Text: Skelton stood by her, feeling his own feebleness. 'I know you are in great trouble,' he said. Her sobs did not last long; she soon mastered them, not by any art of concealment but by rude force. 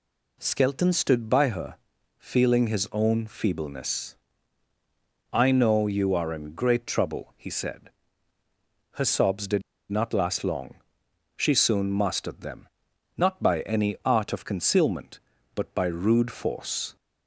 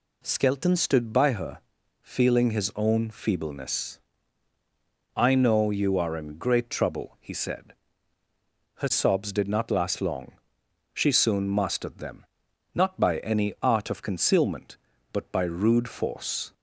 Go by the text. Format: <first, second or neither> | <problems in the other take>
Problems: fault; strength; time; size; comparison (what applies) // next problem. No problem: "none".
second | pauses between "did" and "not"; slight; at 9.6 s; 0.29 s long